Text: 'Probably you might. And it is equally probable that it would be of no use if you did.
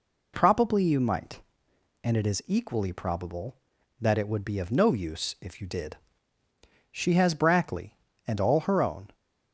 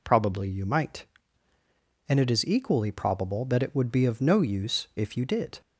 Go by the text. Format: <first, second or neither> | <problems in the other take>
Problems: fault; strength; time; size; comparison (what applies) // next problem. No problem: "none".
second | goes on to say "She has Brackley and all her own"; strong; from 6.9 s on; 2.2 s long